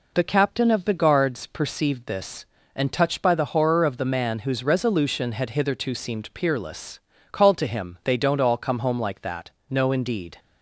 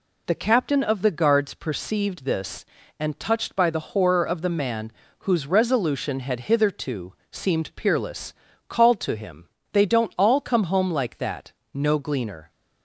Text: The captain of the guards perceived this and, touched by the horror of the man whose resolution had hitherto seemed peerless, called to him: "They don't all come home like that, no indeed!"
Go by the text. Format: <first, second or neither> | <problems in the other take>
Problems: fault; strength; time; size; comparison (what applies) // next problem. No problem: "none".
first | pauses between "man" and "whose"; slight; at 4.9 s; 0.30 s long // pauses between "hitherto" and "seemed"; slight; at 7.1 s; 0.18 s long // says "gleaner" for "indeed"; at 12.0 s